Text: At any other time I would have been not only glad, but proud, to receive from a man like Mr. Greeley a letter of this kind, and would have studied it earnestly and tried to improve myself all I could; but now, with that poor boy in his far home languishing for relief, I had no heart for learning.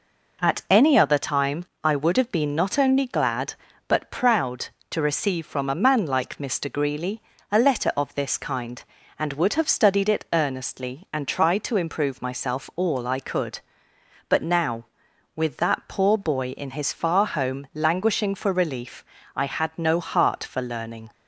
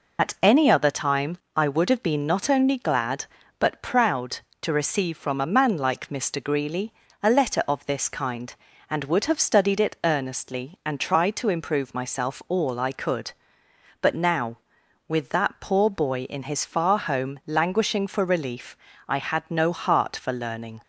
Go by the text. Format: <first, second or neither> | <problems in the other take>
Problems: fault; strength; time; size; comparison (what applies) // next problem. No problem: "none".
first | loses the start of "At"; at 0.1 s; 80 ms // pauses between "time" and "I"; slight; at 1.3 s; 0.18 s long; slight in the first // pauses between "Greeley" and "a"; slight; at 6.9 s; 0.32 s long; slight in the first